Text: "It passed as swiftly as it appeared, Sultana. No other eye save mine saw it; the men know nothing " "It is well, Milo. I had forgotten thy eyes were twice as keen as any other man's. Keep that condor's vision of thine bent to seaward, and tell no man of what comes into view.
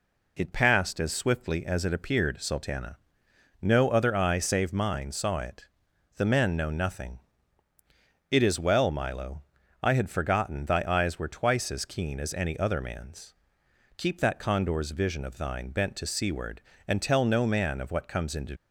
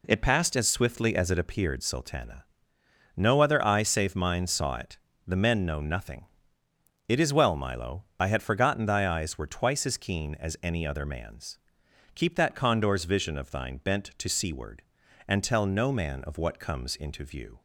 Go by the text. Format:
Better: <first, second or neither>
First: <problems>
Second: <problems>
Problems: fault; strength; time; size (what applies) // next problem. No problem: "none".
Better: second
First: stops before "view"; at 18.5 s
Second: none